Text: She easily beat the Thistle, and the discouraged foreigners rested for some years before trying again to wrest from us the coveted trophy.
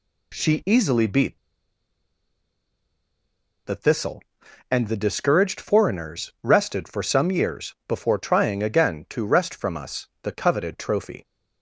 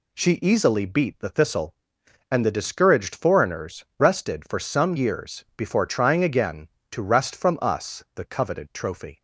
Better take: second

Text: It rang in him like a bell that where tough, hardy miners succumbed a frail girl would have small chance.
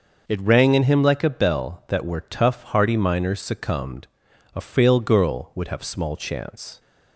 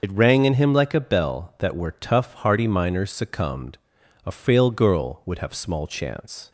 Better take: first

